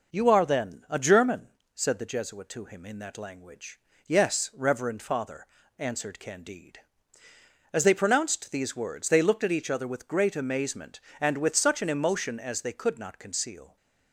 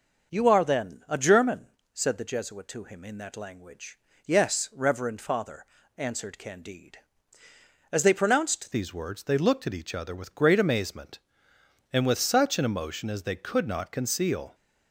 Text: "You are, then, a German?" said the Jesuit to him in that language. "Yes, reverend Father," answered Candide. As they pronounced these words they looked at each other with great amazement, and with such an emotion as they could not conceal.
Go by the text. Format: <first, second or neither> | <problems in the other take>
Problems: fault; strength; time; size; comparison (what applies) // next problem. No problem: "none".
first | changes voice at "these"; from 8.7 s on; 5.8 s long